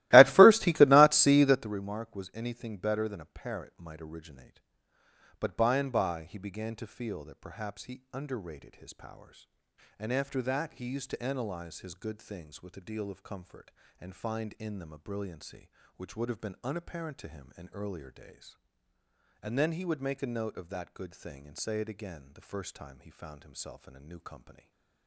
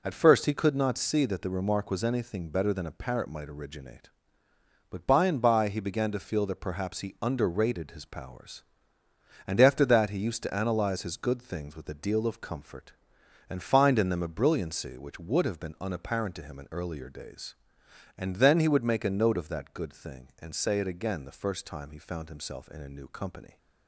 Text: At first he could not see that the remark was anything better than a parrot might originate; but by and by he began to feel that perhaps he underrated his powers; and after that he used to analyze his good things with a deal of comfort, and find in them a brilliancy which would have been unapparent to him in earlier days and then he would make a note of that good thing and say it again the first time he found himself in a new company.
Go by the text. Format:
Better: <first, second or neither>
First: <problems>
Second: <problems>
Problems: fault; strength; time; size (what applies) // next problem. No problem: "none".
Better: second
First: starts louder than the rest; strong; until 1.7 s; 17.5 dB // stays silent after the last word; slight; from 24.5 s on; 0.5 s long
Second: none